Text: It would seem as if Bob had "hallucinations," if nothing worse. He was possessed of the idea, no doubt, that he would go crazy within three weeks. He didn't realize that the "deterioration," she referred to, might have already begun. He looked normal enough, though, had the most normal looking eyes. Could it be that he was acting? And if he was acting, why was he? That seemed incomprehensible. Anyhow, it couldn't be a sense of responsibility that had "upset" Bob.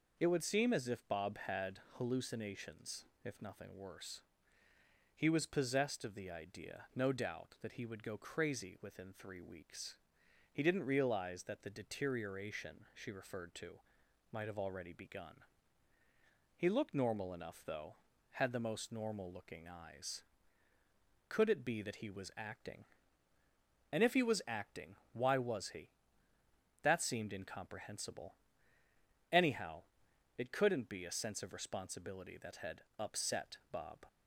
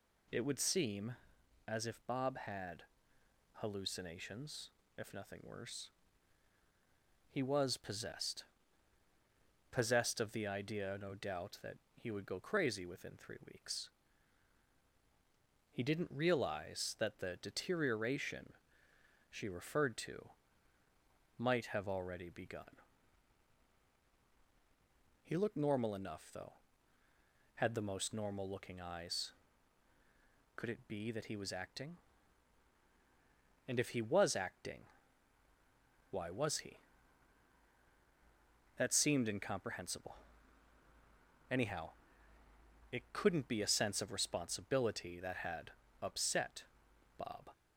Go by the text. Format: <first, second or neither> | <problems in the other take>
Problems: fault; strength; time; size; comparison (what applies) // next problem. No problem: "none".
first | pauses between "had" and "hallucinations"; noticeable; at 2.8 s; 0.72 s long // says "possessed" twice; at 9.7 s // pauses between "that" and "he"; slight; at 11.7 s; 0.18 s long // pauses between "three" and "weeks"; slight; at 13.3 s; 0.16 s long // pauses between "had" and "upset"; slight; at 45.7 s; 0.28 s long; slight in the first // pauses between "upset" and "Bob"; noticeable; at 46.6 s; 0.54 s long